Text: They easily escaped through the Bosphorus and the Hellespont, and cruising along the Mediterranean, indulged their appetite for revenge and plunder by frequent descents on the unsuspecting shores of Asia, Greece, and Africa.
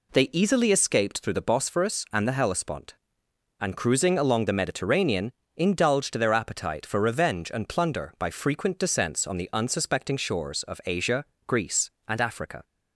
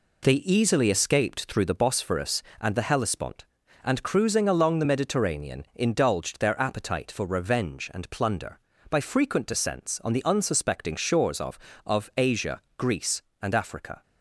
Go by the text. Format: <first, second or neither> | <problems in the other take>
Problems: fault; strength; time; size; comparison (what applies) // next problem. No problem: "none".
first | says "of" twice; at 11.8 s